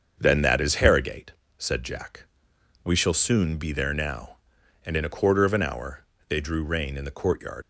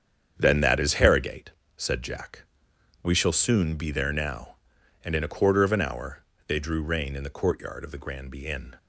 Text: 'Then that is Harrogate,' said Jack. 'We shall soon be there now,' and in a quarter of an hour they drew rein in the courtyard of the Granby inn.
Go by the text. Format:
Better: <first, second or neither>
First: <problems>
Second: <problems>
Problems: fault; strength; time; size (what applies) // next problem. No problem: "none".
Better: second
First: starts louder than the rest; until 1.2 s; 7 dB // pauses between "hour" and "they"; slight; at 6.0 s; 0.24 s long // stops before "of the Granby inn"; at 7.6 s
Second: starts louder than the rest; strong; until 1.4 s; 8 dB // pauses between "hour" and "they"; slight; at 6.2 s; 0.24 s long